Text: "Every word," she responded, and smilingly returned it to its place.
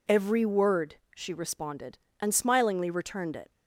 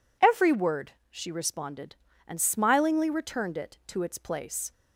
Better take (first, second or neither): second